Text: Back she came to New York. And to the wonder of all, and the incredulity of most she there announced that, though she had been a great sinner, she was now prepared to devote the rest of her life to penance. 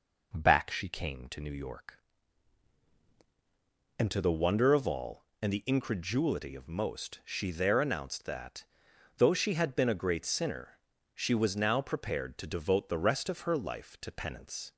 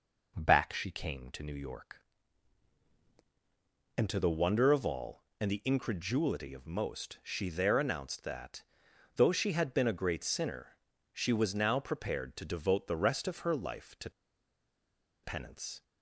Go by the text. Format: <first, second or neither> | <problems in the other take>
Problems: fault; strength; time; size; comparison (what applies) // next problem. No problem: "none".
first | pauses between "to" and "penance"; at 14.0 s; 1.1 s long